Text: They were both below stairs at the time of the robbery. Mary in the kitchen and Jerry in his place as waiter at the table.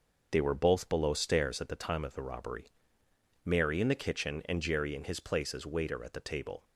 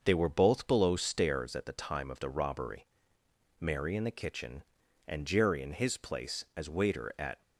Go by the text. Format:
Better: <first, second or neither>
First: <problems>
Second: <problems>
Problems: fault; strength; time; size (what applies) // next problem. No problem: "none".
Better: first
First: none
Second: starts louder than the rest; until 1.0 s; 6.5 dB // stops before "the table"; at 7.4 s